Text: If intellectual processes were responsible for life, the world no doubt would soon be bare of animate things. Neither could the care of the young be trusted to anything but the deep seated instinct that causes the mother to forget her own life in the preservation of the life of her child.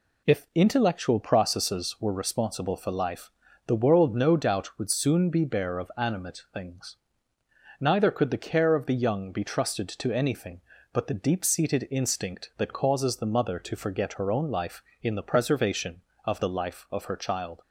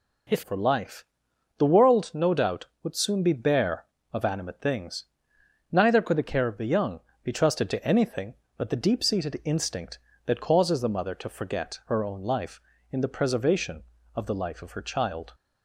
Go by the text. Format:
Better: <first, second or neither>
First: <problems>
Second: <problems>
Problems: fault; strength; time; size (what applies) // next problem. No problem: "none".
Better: first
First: none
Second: skips "intellectual processes were responsible"; at 0.4 s // pauses between "young" and "be"; slight; at 7.0 s; 0.22 s long